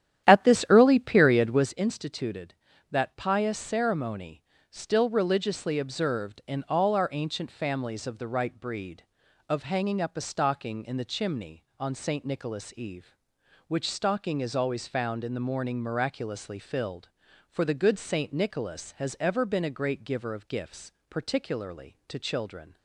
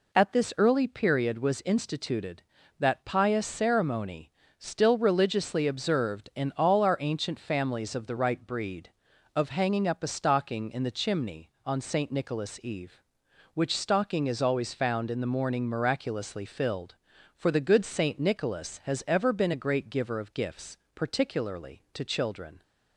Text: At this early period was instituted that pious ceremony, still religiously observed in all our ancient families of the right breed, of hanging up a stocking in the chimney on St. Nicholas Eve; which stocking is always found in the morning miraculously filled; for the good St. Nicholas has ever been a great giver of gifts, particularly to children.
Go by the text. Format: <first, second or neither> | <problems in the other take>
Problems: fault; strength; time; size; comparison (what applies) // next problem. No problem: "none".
second | starts louder than the rest; strong; until 1.8 s; 11 dB